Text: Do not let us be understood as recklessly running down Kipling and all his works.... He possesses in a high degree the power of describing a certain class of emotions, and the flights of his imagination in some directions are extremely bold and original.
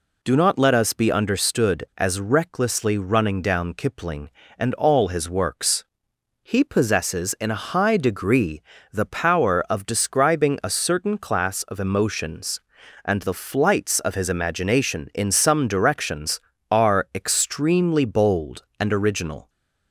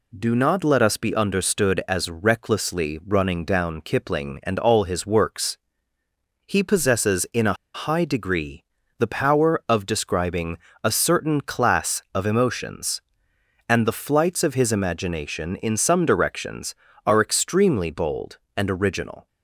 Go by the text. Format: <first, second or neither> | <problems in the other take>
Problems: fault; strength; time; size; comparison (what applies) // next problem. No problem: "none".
first | pauses between "a" and "high"; slight; at 7.5 s; 0.19 s long // pauses between "degree" and "the"; slight; at 8.6 s; 0.34 s long; slight in the first // pauses between "describing" and "a"; slight; at 10.5 s; 0.28 s long